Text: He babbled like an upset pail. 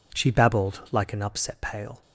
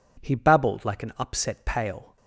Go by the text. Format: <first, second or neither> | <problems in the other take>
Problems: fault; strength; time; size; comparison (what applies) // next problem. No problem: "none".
second | says "She" for "He"; at 0.1 s